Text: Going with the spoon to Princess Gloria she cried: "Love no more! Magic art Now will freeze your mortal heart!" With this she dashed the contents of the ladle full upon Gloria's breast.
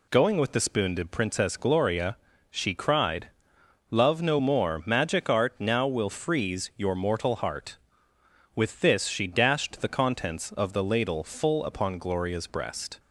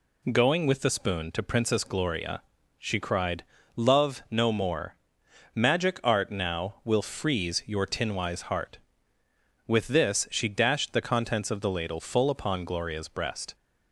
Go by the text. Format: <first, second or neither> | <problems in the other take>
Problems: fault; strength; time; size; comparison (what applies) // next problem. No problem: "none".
first | pauses between "Gloria" and "she"; slight; at 2.4 s; 0.36 s long; slight in the first // says "tinwise" for "mortal"; at 7.8 s